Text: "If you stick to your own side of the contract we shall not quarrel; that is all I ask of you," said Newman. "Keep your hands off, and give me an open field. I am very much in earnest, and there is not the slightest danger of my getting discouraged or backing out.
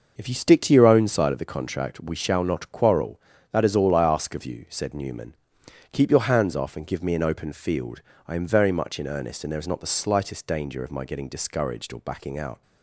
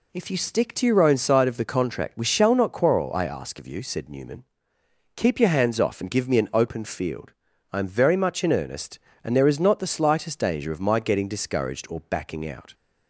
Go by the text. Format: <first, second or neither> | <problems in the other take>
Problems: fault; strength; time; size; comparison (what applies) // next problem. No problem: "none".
first | skips "that is all"; at 3.1 s